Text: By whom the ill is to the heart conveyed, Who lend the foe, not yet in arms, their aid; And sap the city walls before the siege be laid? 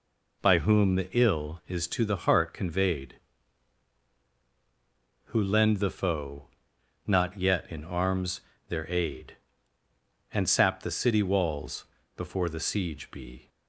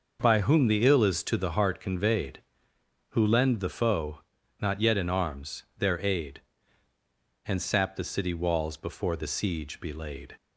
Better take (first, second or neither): second